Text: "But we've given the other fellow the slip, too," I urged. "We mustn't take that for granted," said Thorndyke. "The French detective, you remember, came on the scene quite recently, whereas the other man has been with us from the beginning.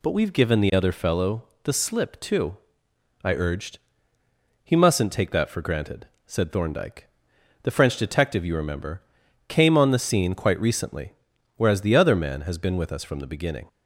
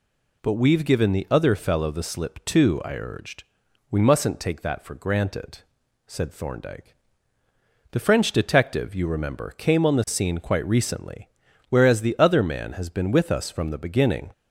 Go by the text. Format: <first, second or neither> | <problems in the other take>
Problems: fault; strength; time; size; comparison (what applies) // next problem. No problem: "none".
second | pauses between "fellow" and "the"; slight; at 1.4 s; 0.20 s long // says "He" for "We"; at 4.6 s